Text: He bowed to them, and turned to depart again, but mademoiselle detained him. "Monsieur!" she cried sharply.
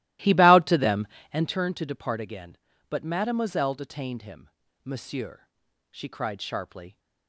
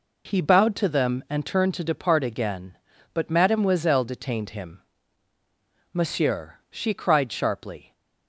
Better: second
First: starts louder than the rest; strong; until 1.6 s; 16.5 dB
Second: none

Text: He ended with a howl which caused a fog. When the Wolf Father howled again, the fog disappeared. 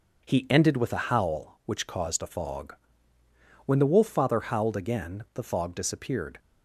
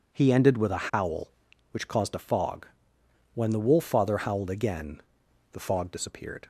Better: neither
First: none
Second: none

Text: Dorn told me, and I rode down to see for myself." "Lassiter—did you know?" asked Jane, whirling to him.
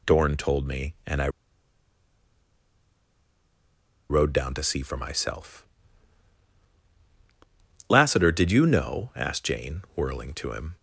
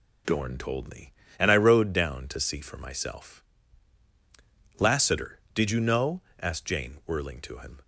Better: second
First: pauses between "I" and "rode"; strong; at 1.2 s; 2.8 s long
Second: none

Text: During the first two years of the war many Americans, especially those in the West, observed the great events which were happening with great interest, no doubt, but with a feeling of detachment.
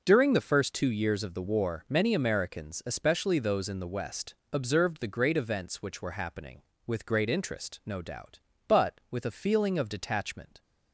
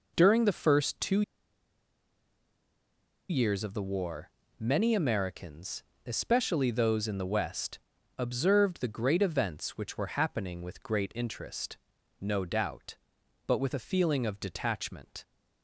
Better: first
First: none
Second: pauses between "two" and "years"; strong; at 1.2 s; 2.0 s long // pauses between "war" and "many"; slight; at 4.3 s; 0.28 s long

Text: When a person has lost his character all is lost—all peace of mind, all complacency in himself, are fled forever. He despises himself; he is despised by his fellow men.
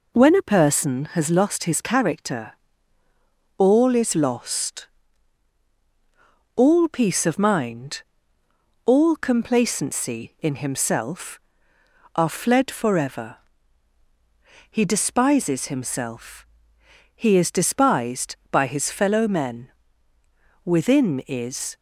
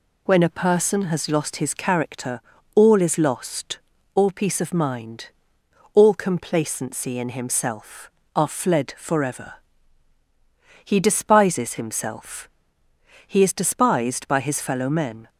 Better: second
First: pauses between "character" and "all"; at 2.5 s; 1.0 s long // goes on to say "Within is"; noticeable; from 20.6 s on; 1.1 s long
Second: pauses between "character" and "all"; slight; at 2.4 s; 0.34 s long

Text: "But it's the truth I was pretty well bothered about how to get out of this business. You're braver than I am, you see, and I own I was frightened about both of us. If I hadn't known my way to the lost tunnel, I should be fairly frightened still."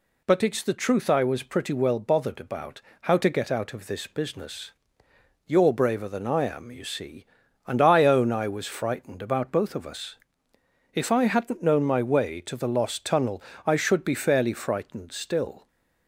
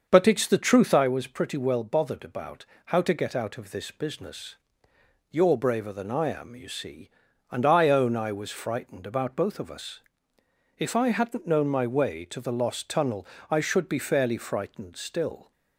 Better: first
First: pauses between "about" and "how"; slight; at 2.8 s; 0.20 s long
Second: starts louder than the rest; until 1.1 s; 6.5 dB // pauses between "about" and "how"; slight; at 2.6 s; 0.20 s long

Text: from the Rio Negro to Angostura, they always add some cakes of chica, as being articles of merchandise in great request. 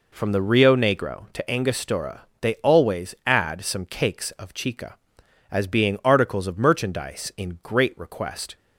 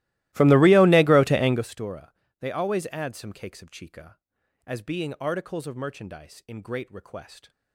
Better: first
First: none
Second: starts louder than the rest; strong; until 1.7 s; 17.5 dB

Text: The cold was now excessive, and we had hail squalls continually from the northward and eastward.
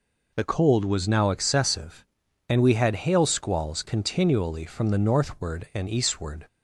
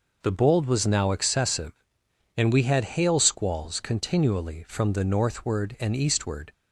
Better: first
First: none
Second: says "bold" for "cold"; at 0.3 s

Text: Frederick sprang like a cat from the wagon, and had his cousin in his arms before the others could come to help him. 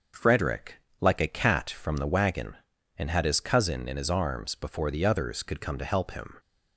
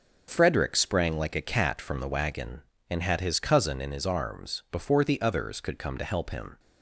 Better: second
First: starts louder than the rest; until 1.3 s; 6.5 dB // skips "sprang"; at 0.8 s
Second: none

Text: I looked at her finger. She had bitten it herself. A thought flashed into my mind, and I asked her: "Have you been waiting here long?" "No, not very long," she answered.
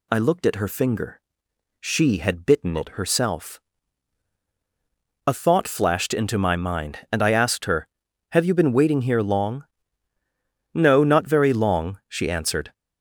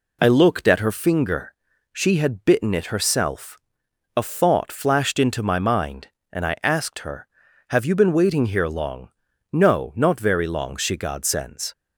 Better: first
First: none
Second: says "godsends" for "answered"; at 10.9 s

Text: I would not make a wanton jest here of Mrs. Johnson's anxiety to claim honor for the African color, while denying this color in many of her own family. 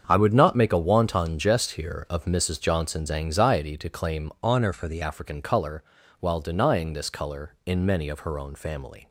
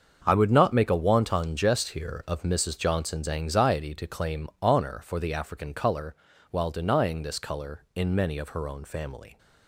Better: second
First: starts louder than the rest; strong; until 1.0 s; 7.5 dB // changes voice from "honor" to "the"; from 4.4 to 5.0 s; 0.6 s long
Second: starts louder than the rest; until 1.2 s; 7 dB

